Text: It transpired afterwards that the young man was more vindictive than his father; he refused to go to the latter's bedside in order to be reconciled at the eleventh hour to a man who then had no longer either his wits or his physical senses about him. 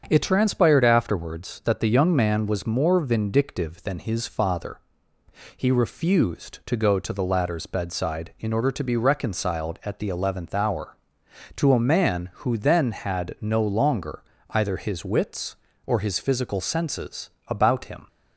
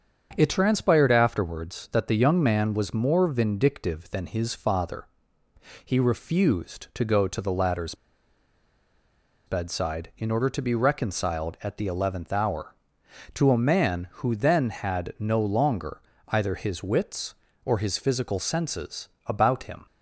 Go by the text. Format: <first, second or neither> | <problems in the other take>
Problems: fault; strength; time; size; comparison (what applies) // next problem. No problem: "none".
first | starts louder than the rest; strong; until 1.3 s; 7.5 dB; strong in the first // pauses between "latter's" and "bedside"; strong; at 7.9 s; 1.5 s long // pauses between "longer" and "either"; slight; at 15.9 s; 0.28 s long; slight in the first // pauses between "senses" and "about"; slight; at 19.0 s; 0.18 s long; slight in the first